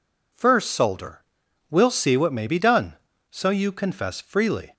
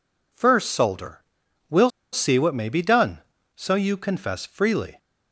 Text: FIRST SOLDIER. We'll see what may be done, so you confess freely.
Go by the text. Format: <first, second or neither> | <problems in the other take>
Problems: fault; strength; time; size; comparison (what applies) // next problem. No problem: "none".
first | pauses between "We'll" and "see"; slight; at 1.8 s; 0.23 s long